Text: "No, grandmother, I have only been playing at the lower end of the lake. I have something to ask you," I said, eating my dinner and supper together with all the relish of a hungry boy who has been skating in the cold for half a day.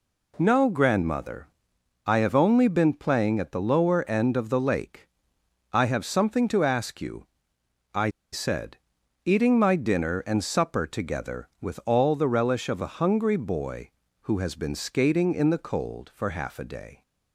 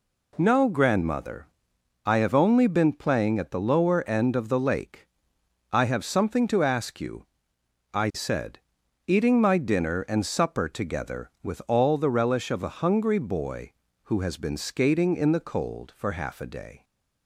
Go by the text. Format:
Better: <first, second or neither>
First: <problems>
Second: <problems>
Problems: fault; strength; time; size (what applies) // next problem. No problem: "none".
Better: second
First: pauses between "I" and "said"; slight; at 8.0 s; 0.23 s long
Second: none